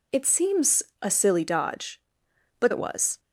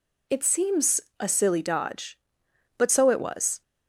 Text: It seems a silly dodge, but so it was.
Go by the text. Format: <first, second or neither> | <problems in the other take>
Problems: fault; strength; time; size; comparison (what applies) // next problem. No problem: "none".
second | pauses between "seems" and "a"; slight; at 0.8 s; 0.18 s long; slight in the second // skips "so"; at 2.7 s